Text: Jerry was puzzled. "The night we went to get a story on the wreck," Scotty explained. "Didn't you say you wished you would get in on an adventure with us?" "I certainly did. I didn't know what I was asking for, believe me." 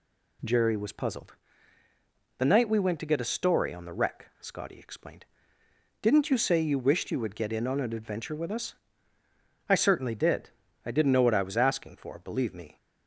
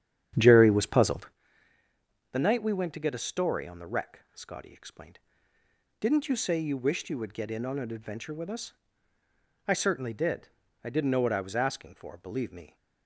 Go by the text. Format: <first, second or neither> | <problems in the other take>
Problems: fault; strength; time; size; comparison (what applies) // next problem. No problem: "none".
first | starts louder than the rest; strong; until 1.4 s; 9.5 dB